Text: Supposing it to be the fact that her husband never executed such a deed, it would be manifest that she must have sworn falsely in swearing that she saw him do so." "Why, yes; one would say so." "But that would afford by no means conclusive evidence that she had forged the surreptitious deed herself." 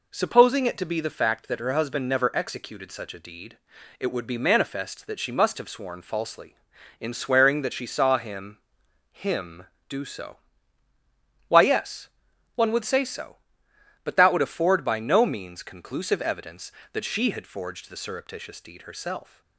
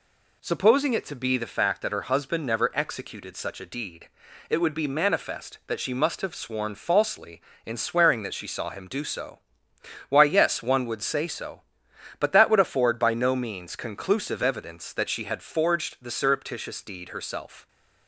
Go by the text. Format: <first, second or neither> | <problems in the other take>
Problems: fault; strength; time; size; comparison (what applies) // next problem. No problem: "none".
second | says "him" twice; at 9.1 s